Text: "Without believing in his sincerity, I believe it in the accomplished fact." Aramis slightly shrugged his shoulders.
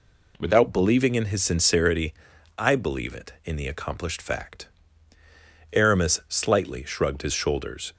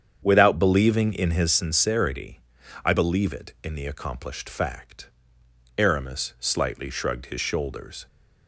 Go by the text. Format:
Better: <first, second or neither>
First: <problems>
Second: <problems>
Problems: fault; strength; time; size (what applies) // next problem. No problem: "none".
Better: first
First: none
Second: starts louder than the rest; strong; until 1.5 s; 8 dB